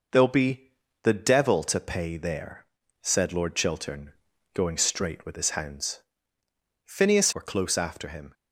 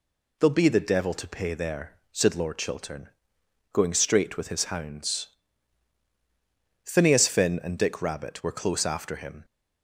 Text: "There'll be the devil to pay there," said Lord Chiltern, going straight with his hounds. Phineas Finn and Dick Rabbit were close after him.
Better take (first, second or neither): second